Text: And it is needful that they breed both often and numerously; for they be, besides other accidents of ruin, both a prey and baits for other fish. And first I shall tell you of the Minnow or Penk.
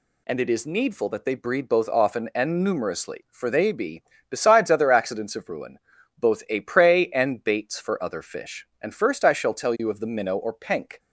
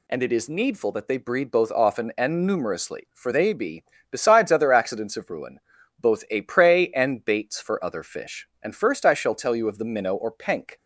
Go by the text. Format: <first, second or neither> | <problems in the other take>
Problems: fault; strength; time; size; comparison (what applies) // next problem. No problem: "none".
neither | none